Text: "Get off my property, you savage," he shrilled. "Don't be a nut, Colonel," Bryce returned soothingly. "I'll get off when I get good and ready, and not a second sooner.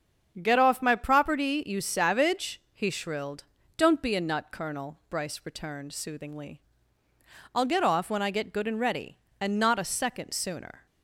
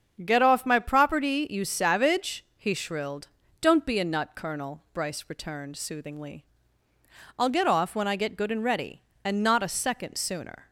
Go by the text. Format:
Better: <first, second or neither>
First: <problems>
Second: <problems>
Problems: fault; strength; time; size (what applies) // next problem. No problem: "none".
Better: neither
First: starts louder than the rest; strong; until 1.4 s; 7.5 dB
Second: starts louder than the rest; strong; until 1.2 s; 7.5 dB